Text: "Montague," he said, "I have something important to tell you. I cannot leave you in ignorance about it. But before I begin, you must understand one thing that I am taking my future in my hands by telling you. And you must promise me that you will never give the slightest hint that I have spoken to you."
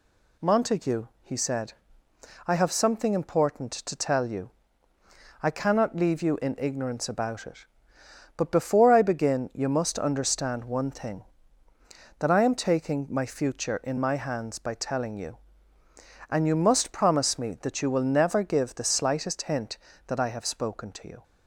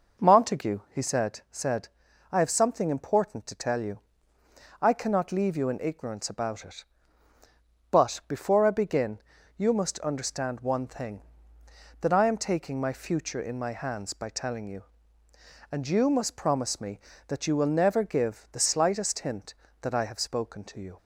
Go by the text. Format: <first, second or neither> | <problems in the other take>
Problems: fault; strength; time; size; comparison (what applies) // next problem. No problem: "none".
first | says "said" twice; at 1.5 s